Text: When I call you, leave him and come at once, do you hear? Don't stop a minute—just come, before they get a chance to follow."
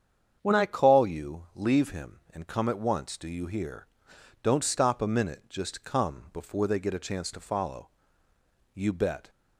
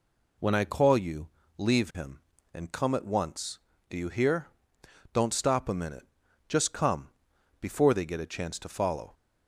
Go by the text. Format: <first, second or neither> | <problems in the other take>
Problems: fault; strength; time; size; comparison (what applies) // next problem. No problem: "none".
second | starts louder than the rest; strong; until 1.4 s; 7.5 dB // goes on to say "You bet"; from 8.7 s on; 0.54 s long